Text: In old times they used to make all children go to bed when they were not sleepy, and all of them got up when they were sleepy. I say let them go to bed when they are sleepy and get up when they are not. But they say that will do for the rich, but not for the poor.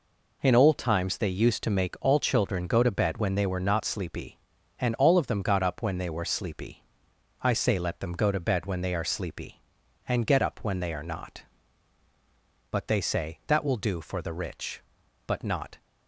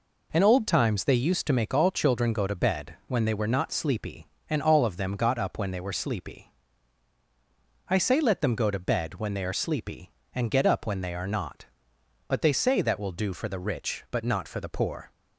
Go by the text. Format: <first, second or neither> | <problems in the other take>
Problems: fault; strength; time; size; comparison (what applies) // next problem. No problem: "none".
second | stops before "for the poor"; at 15.7 s